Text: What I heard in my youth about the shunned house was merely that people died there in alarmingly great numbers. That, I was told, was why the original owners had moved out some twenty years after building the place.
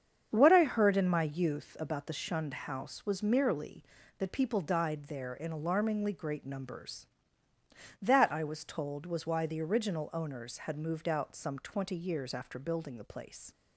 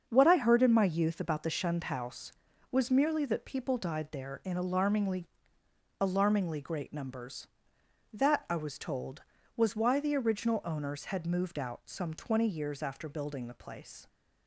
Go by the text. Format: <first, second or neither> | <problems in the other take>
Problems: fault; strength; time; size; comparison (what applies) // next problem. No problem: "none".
first | starts louder than the rest; until 1.1 s; 7 dB; strong in the first // says "alarmingly" twice; at 5.9 s